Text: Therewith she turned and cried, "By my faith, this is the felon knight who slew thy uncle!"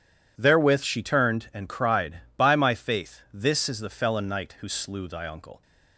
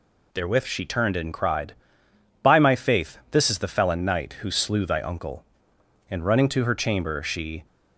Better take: first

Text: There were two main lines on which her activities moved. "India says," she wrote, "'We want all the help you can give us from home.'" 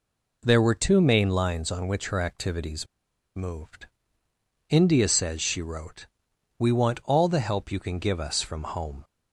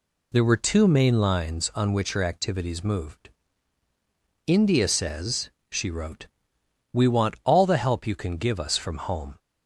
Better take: second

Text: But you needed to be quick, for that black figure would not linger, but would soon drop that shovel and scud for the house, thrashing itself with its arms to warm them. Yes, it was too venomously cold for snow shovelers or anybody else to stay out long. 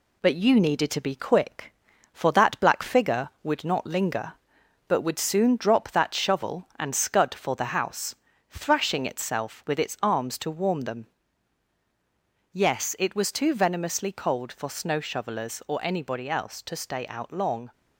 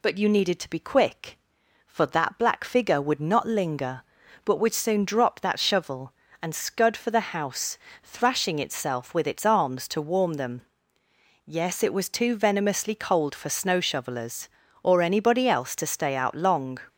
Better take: second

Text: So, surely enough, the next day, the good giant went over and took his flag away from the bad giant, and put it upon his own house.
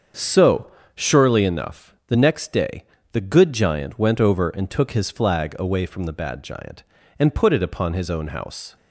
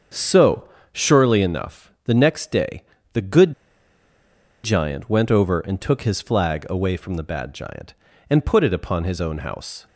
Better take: first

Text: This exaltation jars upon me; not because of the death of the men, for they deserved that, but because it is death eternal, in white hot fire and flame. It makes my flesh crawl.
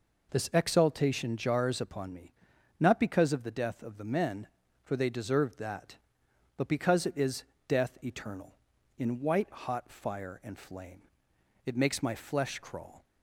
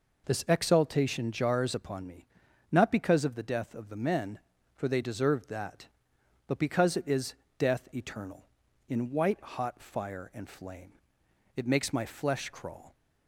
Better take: neither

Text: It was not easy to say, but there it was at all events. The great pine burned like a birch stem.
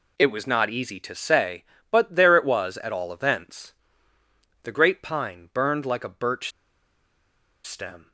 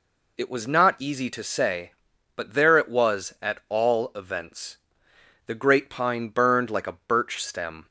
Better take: second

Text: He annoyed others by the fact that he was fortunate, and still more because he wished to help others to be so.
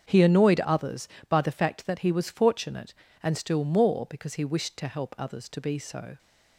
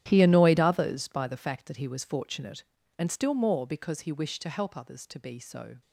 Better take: first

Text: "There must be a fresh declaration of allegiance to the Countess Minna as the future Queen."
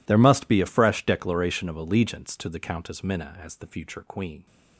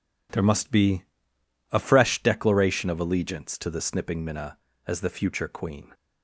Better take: first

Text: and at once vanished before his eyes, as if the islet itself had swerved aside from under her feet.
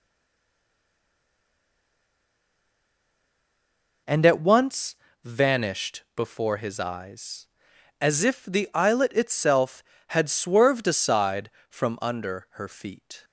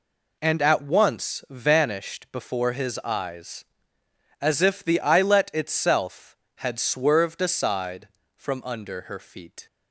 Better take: second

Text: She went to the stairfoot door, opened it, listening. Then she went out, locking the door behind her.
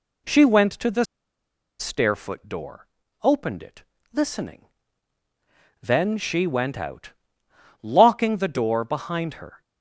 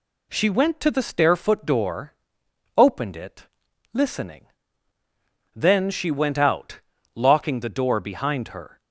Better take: second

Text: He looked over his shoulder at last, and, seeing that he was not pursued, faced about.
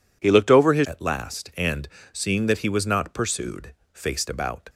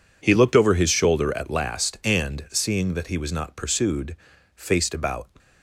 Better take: second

